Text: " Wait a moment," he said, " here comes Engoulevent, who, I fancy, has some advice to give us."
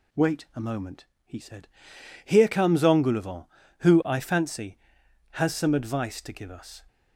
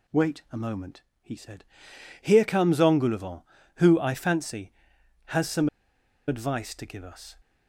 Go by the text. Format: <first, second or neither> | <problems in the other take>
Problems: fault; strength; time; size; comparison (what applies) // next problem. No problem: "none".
first | pauses between "some" and "advice"; noticeable; at 5.6 s; 0.59 s long